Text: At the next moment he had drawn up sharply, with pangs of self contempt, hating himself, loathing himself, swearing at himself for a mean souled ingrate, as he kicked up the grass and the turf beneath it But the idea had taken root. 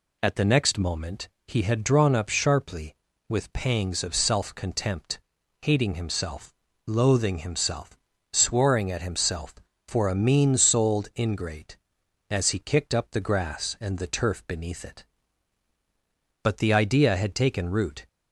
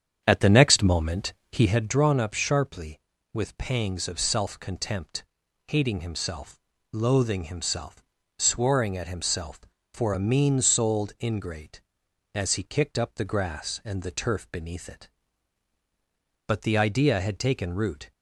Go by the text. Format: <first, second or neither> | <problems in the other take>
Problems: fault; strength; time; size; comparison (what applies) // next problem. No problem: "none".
first | starts louder than the rest; strong; until 1.9 s; 8.5 dB // pauses between "moment" and "he"; slight; at 1.3 s; 0.18 s long; slight in the first